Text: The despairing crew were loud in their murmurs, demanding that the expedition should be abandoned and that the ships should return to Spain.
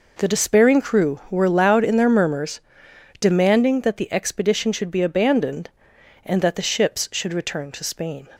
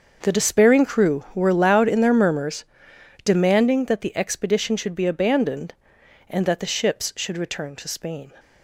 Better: first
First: none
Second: gets quieter; strong; throughout; 14 dB

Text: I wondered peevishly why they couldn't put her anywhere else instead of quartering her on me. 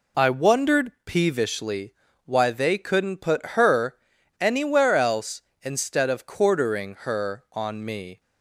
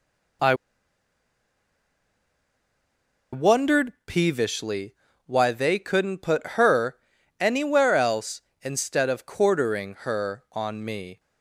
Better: first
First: pauses between "peevishly" and "why"; slight; at 1.9 s; 0.32 s long // pauses between "her" and "anywhere"; at 3.9 s; 0.45 s long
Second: pauses between "I" and "wondered"; strong; at 0.5 s; 2.7 s long // pauses between "peevishly" and "why"; slight; at 4.9 s; 0.32 s long // pauses between "her" and "anywhere"; at 6.9 s; 0.44 s long

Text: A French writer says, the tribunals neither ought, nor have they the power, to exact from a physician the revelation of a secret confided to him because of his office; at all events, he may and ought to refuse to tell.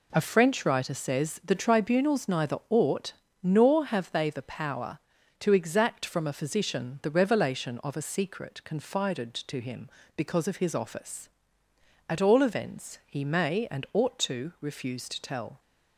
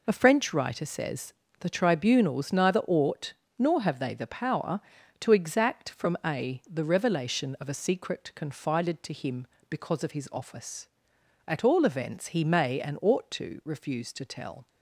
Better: first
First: none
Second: skips "physician"; at 6.6 s

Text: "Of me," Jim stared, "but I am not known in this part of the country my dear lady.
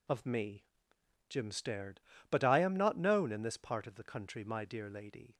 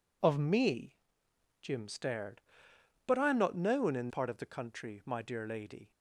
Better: first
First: none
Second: skips "this"; at 4.0 s

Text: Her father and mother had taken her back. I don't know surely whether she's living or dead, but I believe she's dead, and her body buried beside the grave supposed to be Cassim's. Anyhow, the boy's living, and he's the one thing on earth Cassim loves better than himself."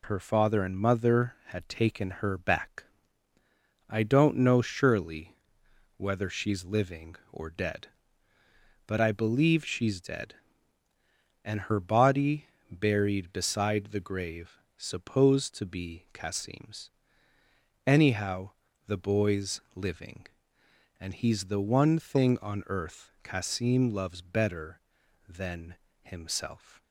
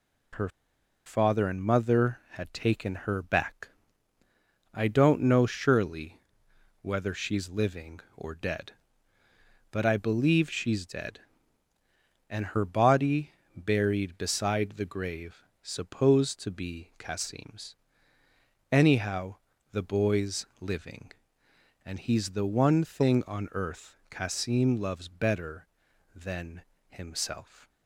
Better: first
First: pauses between "surely" and "whether"; noticeable; at 5.3 s; 0.62 s long // pauses between "body" and "buried"; slight; at 12.4 s; 0.22 s long // pauses between "grave" and "supposed"; slight; at 14.5 s; 0.18 s long // pauses between "than" and "himself"; slight; at 25.7 s; 0.26 s long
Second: pauses between "Her" and "father"; noticeable; at 0.4 s; 0.58 s long // pauses between "surely" and "whether"; noticeable; at 6.1 s; 0.62 s long // pauses between "body" and "buried"; slight; at 13.3 s; 0.22 s long // pauses between "grave" and "supposed"; slight; at 15.4 s; 0.18 s long // pauses between "than" and "himself"; slight; at 26.6 s; 0.26 s long

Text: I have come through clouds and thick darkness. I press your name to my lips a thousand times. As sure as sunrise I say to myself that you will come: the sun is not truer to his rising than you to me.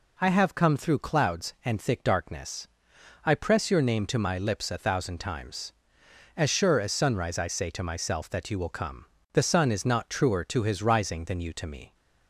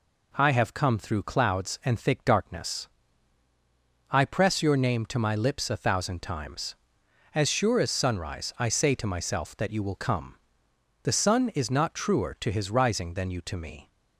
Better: neither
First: none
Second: none

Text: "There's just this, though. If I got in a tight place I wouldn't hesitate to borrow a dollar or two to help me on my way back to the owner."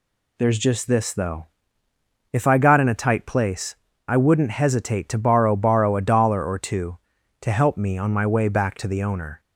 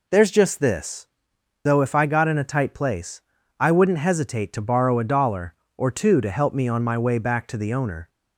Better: second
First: pauses between "place" and "I"; slight; at 3.7 s; 0.30 s long // says "borrow" twice; at 5.5 s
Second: pauses between "place" and "I"; at 3.2 s; 0.38 s long

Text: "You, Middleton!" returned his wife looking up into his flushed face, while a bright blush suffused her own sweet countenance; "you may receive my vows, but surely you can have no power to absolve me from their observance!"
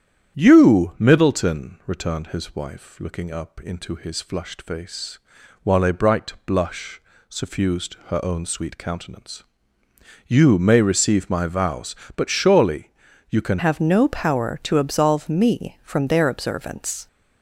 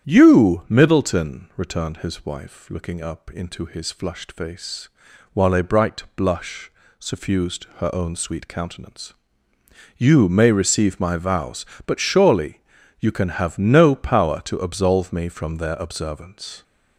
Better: second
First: starts louder than the rest; strong; until 1.4 s; 9.5 dB // pauses between "blush" and "suffused"; slight; at 7.0 s; 0.28 s long // pauses between "surely" and "you"; at 12.9 s; 0.40 s long // changes voice at "have"; from 13.5 s on; 3.5 s long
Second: starts louder than the rest; strong; until 1.1 s; 9.5 dB // pauses between "blush" and "suffused"; slight; at 6.7 s; 0.28 s long // pauses between "surely" and "you"; at 12.6 s; 0.40 s long

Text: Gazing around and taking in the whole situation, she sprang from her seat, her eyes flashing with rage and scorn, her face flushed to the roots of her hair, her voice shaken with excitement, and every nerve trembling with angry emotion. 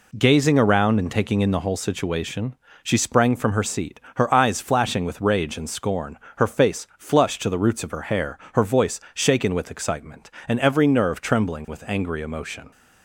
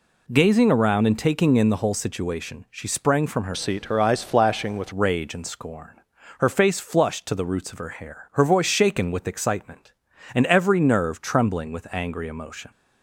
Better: first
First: none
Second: changes voice from "seat" to "with"; from 3.5 to 4.9 s; 1.4 s long

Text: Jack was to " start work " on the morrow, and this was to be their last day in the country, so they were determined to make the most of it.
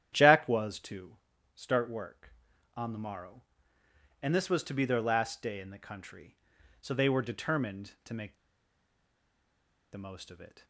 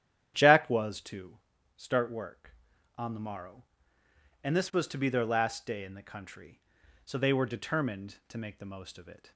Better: second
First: starts louder than the rest; strong; until 1.1 s; 10 dB // pauses between "make" and "the"; strong; at 8.3 s; 1.5 s long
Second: starts louder than the rest; strong; until 1.3 s; 10 dB

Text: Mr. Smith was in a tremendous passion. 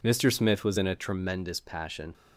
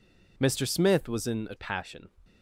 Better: first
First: none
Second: skips "tremendous"; at 1.5 s

